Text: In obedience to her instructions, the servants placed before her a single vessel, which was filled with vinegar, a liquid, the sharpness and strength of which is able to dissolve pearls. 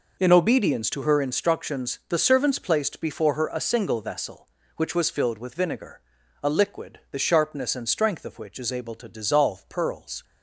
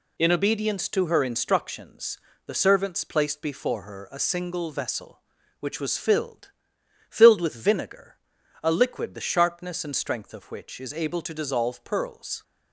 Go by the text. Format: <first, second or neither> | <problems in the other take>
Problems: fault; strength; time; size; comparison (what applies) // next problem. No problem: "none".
first | says "filled" twice; at 7.1 s